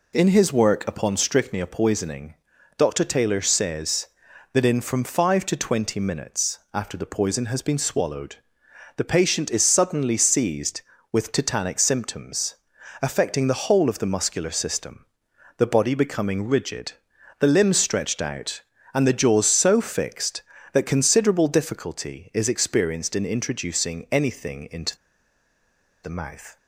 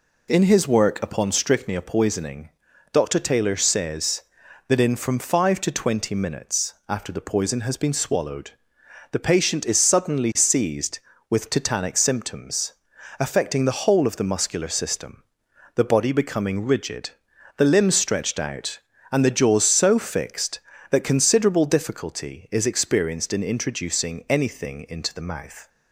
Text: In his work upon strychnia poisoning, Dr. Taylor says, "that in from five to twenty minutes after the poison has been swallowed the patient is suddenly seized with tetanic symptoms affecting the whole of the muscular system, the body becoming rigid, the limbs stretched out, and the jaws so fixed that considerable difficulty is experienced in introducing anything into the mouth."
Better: second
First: pauses between "swallowed" and "the"; noticeable; at 8.3 s; 0.58 s long // pauses between "symptoms" and "affecting"; noticeable; at 12.5 s; 0.48 s long // pauses between "into" and "the"; at 24.9 s; 1.0 s long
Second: pauses between "swallowed" and "the"; noticeable; at 8.5 s; 0.58 s long // pauses between "symptoms" and "affecting"; noticeable; at 12.7 s; 0.48 s long

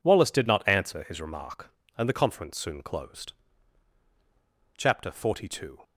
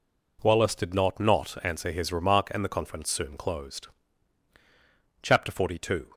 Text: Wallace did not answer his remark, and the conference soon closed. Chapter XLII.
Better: first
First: none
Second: says "not" twice; at 1.1 s

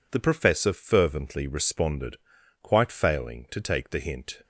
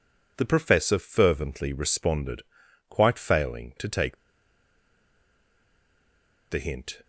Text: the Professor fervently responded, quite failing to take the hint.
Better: first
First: none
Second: pauses between "take" and "the"; strong; at 4.1 s; 2.3 s long

